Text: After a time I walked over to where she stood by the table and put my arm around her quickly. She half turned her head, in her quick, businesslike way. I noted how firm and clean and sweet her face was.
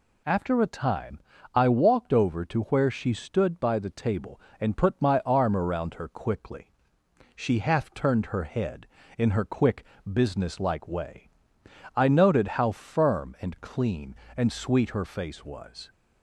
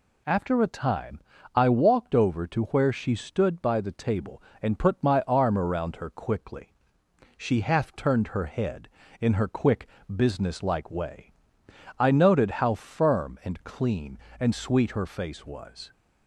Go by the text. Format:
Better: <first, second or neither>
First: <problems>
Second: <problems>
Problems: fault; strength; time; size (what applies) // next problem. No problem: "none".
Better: neither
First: pauses between "time" and "I"; slight; at 1.1 s; 0.36 s long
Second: pauses between "time" and "I"; slight; at 1.1 s; 0.36 s long